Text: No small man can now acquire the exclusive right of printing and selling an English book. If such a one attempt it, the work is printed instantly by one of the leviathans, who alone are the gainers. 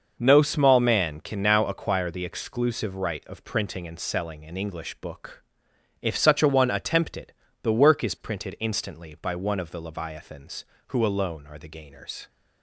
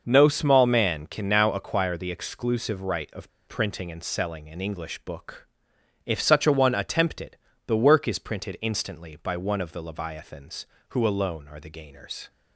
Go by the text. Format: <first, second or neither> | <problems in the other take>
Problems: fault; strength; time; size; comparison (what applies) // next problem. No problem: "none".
first | pauses between "of" and "printing"; slight; at 3.2 s; 0.17 s long